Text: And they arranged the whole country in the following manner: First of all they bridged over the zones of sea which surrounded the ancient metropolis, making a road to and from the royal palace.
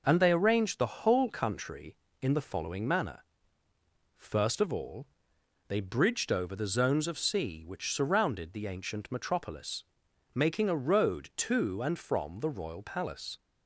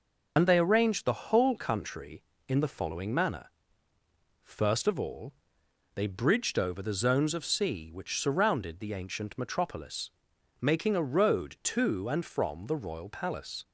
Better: first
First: pauses between "all" and "they"; noticeable; at 5.0 s; 0.60 s long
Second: loses the start of "And"; at 0.3 s; 55 ms // pauses between "all" and "they"; noticeable; at 5.3 s; 0.60 s long

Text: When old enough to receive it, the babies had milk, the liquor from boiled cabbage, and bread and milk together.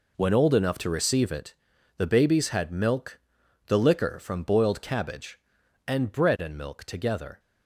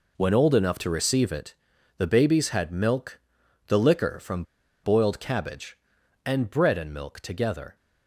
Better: first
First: none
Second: pauses between "from" and "boiled"; at 4.4 s; 0.40 s long

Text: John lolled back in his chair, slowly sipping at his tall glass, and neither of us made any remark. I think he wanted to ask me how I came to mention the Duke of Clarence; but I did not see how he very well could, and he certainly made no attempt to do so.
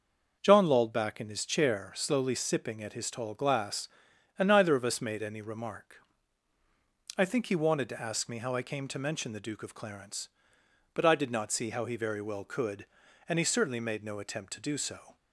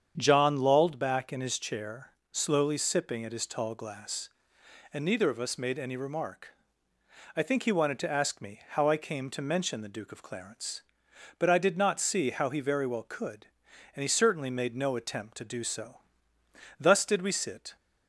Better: first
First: starts louder than the rest; noticeable; until 1.4 s; 6 dB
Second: starts louder than the rest; strong; until 1.1 s; 8 dB // goes on to say "Thus did we sit"; noticeable; from 16.7 s on; 0.96 s long

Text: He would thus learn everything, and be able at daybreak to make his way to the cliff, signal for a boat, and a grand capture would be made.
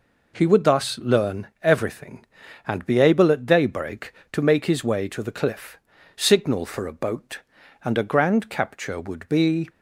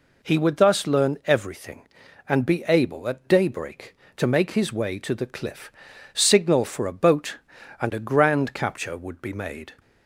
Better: second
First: stops before "made"; at 9.6 s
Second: none

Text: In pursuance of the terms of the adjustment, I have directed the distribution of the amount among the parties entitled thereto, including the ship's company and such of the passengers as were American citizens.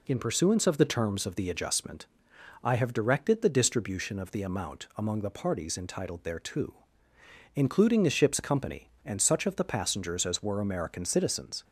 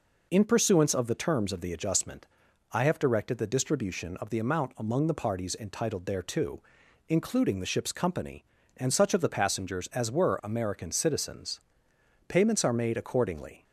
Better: first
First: none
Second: goes on to say "Payments are made accordingly"; from 12.2 s on; 1.3 s long

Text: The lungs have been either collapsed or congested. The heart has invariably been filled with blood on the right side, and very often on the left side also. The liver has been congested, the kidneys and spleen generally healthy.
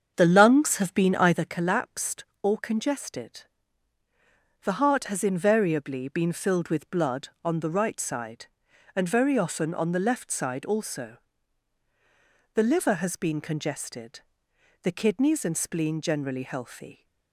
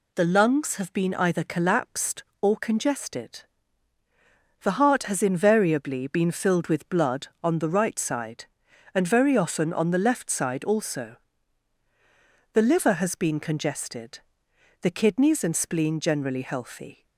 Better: second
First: starts louder than the rest; strong; until 1.5 s; 7 dB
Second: none

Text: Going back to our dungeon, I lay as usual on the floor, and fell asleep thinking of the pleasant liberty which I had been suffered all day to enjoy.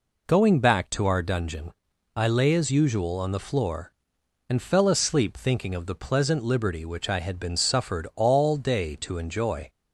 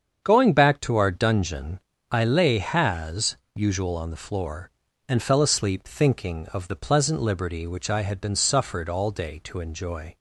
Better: first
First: none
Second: starts louder than the rest; strong; until 1.2 s; 7.5 dB // says "has" for "as"; at 2.5 s

